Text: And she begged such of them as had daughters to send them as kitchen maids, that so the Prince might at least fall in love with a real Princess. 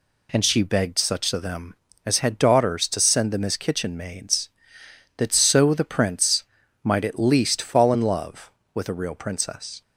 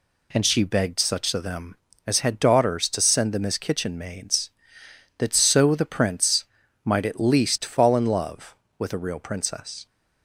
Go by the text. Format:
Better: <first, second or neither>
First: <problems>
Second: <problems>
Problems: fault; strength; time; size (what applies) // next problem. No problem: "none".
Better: neither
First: pauses between "Prince" and "might"; at 6.4 s; 0.38 s long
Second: pauses between "Prince" and "might"; at 6.4 s; 0.38 s long